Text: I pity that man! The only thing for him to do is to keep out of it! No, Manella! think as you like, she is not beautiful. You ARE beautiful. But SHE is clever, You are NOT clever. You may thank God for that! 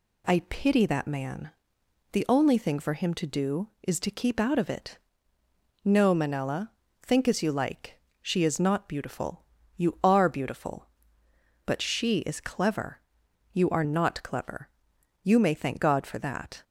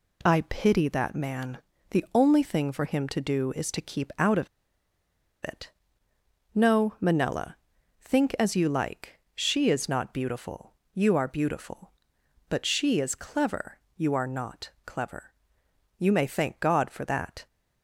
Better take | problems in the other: first | pauses between "of" and "it"; noticeable; at 4.4 s; 0.95 s long

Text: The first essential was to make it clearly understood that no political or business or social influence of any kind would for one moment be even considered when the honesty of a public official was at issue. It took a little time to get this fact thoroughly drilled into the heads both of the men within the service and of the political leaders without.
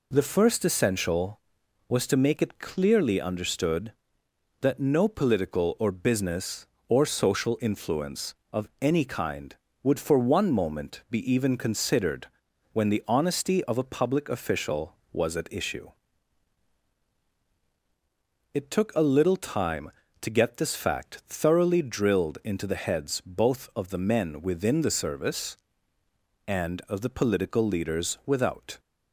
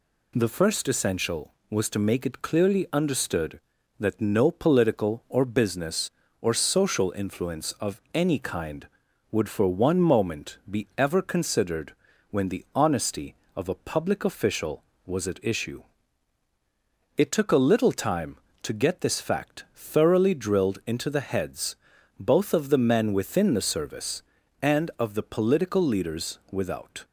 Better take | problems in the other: first | says "ever" for "even"; at 10.9 s // pauses between "considered" and "when"; at 11.9 s; 0.38 s long; noticeable in the first // pauses between "heads" and "both"; at 21.7 s; 0.42 s long

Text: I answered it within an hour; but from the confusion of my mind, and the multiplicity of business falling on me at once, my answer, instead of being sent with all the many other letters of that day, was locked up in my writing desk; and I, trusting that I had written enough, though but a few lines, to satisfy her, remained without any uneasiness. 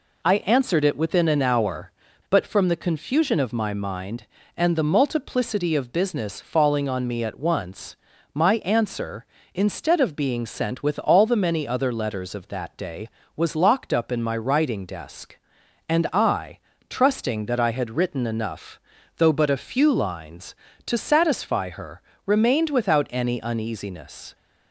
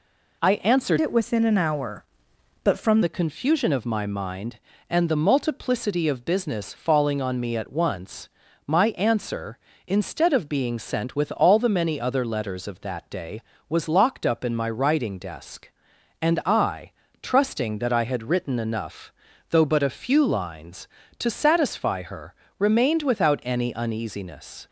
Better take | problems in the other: first | changes voice from "it" to "from"; from 1.0 to 3.0 s; 2.0 s long

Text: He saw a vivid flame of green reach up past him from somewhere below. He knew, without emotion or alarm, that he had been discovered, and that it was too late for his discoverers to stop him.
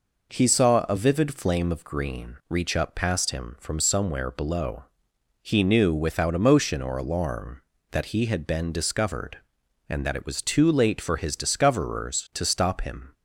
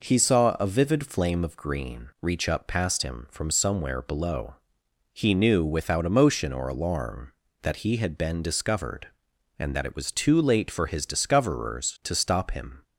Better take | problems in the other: neither | none

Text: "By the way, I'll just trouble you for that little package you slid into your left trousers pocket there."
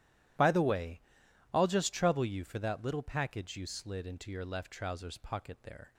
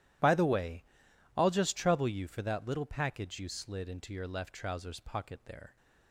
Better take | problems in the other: neither | none

